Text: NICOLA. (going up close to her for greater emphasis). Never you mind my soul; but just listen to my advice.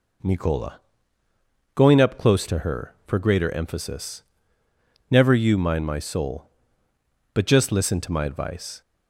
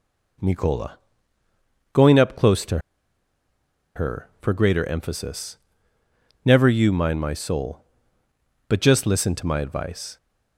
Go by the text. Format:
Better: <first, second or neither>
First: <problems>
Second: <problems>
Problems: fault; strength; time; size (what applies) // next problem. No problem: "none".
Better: first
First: none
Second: pauses between "to" and "her"; at 2.7 s; 1.1 s long